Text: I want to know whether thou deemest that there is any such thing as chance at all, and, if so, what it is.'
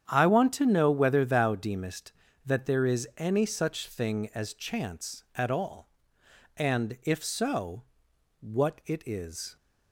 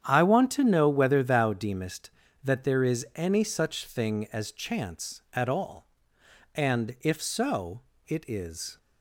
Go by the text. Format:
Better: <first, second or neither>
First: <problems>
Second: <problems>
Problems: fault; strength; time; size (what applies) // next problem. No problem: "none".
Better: first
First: starts louder than the rest; strong; until 1.1 s; 9 dB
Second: starts louder than the rest; strong; until 1.0 s; 9 dB // skips "what"; at 7.9 s